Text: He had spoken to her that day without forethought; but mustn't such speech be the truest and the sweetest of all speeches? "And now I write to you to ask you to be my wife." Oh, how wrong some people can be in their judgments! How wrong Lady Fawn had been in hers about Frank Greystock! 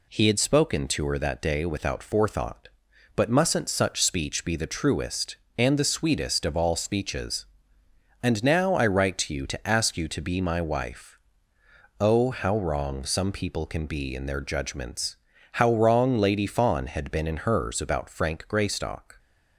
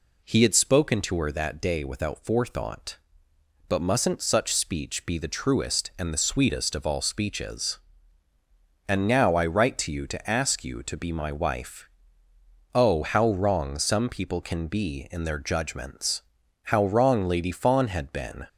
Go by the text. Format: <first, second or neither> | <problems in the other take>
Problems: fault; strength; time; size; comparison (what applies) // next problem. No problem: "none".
first | stops before "in hers about Frank Greystock"; at 18.4 s